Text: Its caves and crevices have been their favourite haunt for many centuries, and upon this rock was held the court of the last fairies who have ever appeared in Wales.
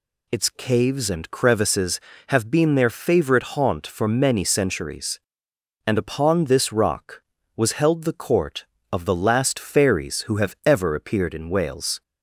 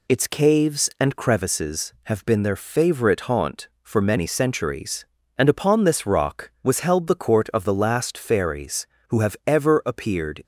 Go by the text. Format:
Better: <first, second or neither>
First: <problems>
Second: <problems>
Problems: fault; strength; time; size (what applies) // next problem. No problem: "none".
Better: first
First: none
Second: stops before "in Wales"; at 10.4 s